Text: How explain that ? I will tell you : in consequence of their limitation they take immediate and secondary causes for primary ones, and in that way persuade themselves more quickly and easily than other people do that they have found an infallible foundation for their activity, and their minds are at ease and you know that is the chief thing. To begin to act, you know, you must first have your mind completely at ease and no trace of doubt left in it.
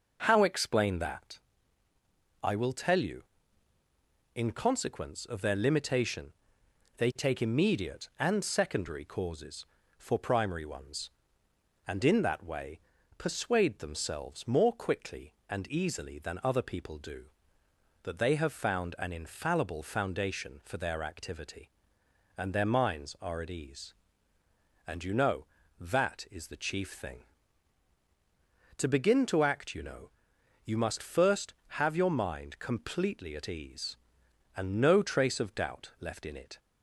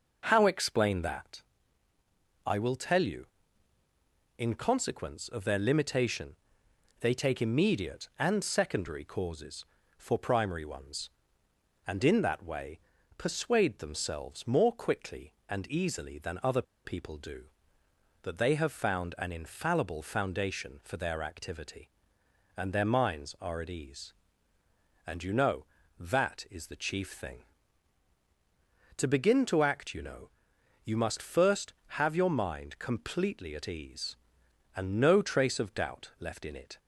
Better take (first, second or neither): first